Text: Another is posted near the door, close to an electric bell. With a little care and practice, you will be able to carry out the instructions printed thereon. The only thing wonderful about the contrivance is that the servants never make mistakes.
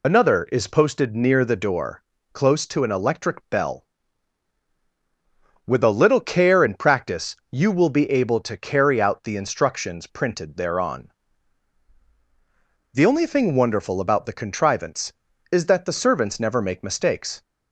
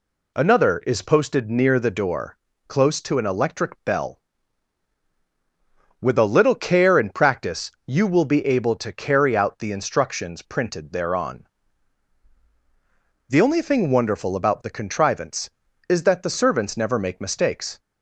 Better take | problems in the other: second | loses the start of "Another"; at 0.0 s; 45 ms

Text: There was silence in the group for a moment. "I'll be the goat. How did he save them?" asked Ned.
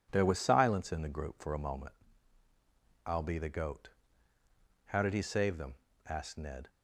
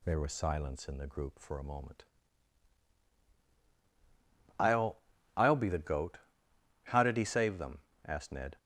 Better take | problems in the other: first | says "I'll" twice; at 5.3 s

